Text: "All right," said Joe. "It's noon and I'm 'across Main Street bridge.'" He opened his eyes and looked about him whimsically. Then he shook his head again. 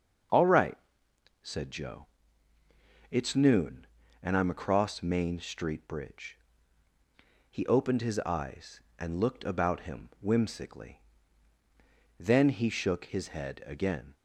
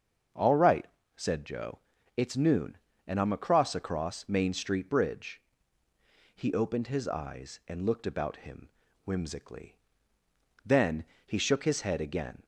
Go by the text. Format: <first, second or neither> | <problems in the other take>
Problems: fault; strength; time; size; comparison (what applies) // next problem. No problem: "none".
first | starts louder than the rest; until 1.6 s; 6.5 dB; also in the first // says "across" twice; at 3.7 s // pauses between "him" and "whimsically"; slight; at 8.6 s; 0.34 s long // pauses between "Then" and "he"; slight; at 11.0 s; 0.22 s long